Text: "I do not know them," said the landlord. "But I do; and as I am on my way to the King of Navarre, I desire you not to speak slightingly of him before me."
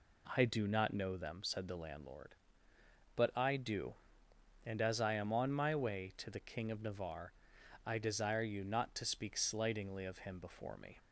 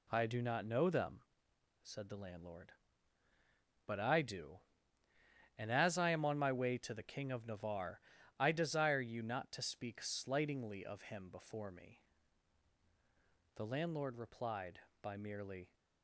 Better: first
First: none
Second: goes on to say "The landlord replied by merely"; strong; from 13.5 s on; 2.1 s long

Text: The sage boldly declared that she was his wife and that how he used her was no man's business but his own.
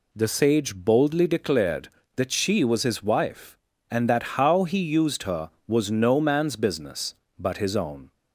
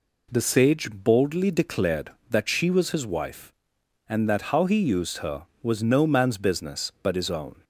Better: neither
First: none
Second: none

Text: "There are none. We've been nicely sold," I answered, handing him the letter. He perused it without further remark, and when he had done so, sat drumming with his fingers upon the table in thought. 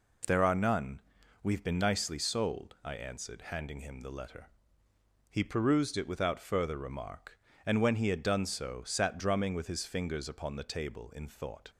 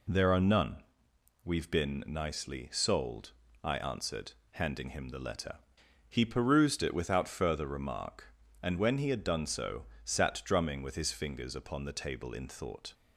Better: neither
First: none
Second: none

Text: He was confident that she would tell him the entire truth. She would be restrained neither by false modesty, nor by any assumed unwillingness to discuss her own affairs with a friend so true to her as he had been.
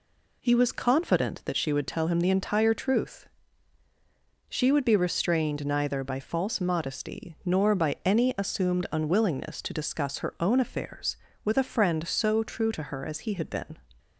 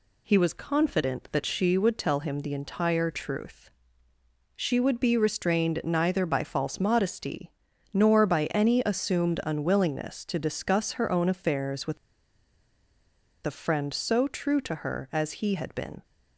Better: first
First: none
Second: pauses between "with" and "a"; strong; at 11.9 s; 1.4 s long

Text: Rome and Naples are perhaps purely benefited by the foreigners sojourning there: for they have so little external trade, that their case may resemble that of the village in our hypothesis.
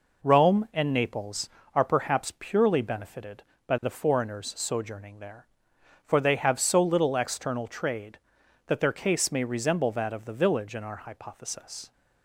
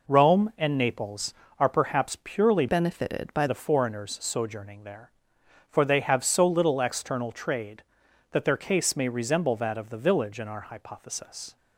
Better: first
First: none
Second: changes voice from "benefited" to "by"; from 2.6 to 3.4 s; 0.8 s long

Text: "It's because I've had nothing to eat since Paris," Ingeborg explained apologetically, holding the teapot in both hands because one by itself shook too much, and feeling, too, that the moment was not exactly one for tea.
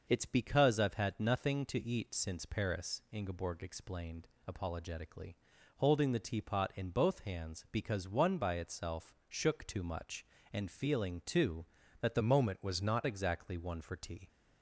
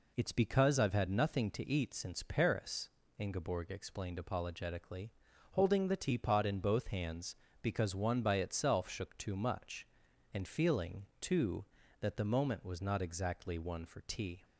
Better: second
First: pauses between "explained" and "apologetically"; slight; at 4.2 s; 0.16 s long // changes voice from "moment" to "not"; from 12.1 to 13.0 s; 0.9 s long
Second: none

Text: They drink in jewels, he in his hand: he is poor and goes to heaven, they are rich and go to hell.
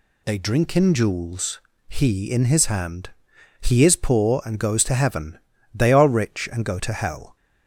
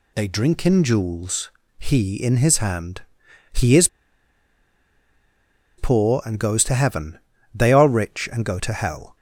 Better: first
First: none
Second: pauses between "is" and "poor"; strong; at 3.8 s; 1.9 s long

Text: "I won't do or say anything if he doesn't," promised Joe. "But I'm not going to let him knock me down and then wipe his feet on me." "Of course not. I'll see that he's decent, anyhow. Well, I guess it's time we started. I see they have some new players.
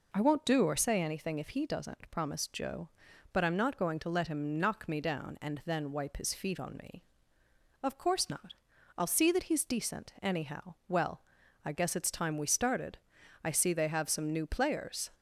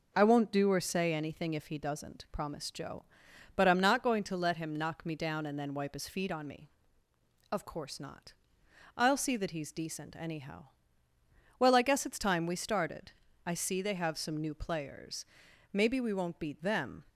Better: first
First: none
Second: goes on to say "Maybe we won't beat them"; from 15.7 s on; 1.3 s long

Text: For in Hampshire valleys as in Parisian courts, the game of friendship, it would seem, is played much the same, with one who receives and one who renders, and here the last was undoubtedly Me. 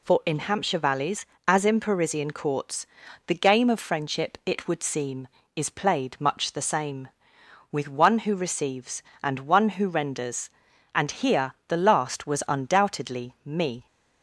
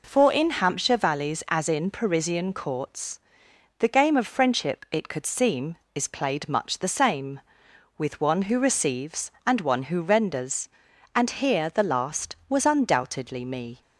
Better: first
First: none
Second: says "could" for "would"; at 5.0 s

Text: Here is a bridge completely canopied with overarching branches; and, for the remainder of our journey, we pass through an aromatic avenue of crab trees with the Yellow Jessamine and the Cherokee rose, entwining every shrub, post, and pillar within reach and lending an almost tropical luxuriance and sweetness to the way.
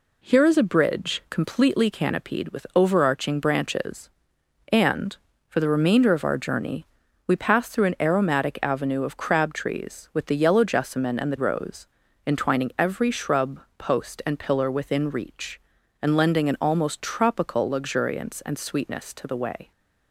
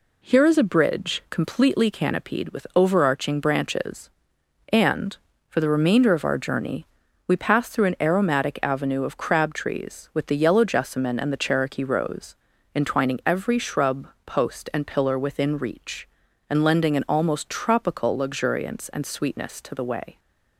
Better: second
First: skips "Cherokee"; at 11.3 s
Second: none

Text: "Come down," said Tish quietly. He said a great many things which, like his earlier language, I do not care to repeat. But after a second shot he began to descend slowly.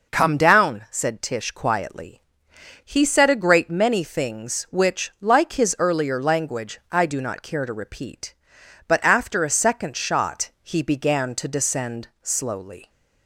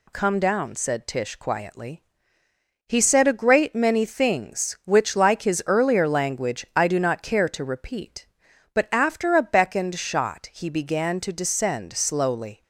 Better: first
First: none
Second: says "beckoned" for "second"; at 9.4 s

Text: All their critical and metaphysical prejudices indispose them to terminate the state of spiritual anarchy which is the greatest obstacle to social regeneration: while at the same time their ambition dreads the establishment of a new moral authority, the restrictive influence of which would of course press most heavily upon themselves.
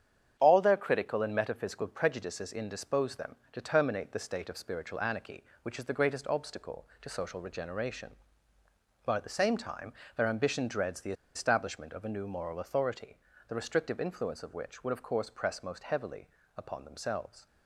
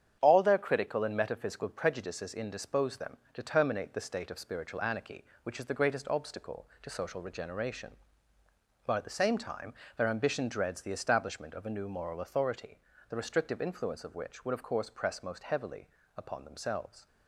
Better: second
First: starts louder than the rest; strong; until 1.3 s; 8.5 dB // pauses between "time" and "their"; slight; at 9.9 s; 0.22 s long // pauses between "the" and "establishment"; slight; at 11.1 s; 0.20 s long // pauses between "heavily" and "upon"; slight; at 16.2 s; 0.30 s long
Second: starts louder than the rest; strong; until 1.2 s; 9 dB // pauses between "time" and "their"; slight; at 9.7 s; 0.22 s long // pauses between "heavily" and "upon"; slight; at 15.8 s; 0.30 s long

